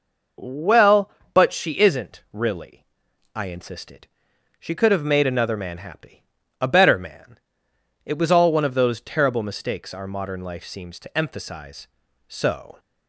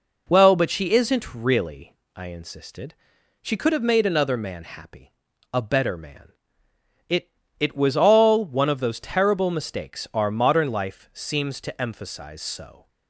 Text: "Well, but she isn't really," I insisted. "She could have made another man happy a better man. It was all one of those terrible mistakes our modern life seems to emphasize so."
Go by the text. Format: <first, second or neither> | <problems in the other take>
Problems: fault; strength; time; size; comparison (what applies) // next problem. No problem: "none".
first | pauses between "happy" and "a"; at 5.1 s; 0.40 s long; also in the first // says "It" twice; at 7.5 s